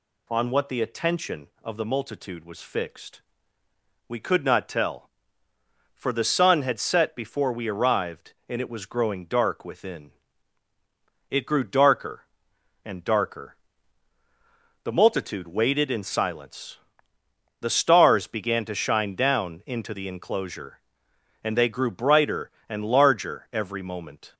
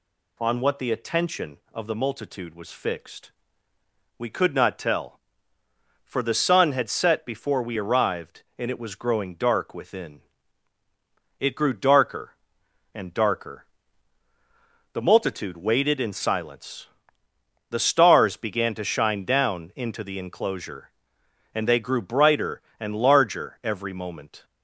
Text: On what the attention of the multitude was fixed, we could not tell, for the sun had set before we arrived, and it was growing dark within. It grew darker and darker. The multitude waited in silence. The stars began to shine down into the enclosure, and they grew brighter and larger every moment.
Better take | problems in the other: neither | none

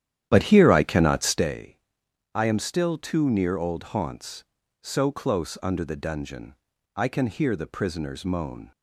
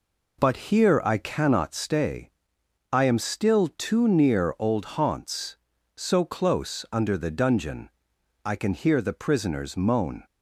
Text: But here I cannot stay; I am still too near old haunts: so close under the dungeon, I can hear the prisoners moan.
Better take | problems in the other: second | starts louder than the rest; strong; until 1.5 s; 10.5 dB

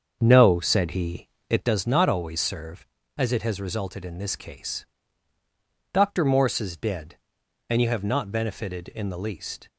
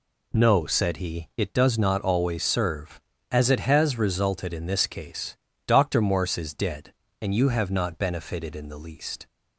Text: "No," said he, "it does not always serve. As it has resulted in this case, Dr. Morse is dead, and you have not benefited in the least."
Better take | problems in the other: second | starts louder than the rest; until 1.7 s; 7 dB

